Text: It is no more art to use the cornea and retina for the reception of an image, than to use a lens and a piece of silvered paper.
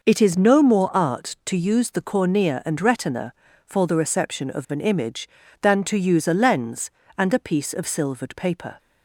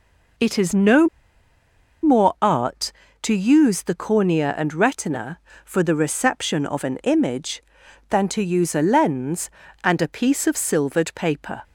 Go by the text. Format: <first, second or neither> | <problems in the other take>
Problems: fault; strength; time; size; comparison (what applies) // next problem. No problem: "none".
first | pauses between "no" and "more"; noticeable; at 1.0 s; 0.96 s long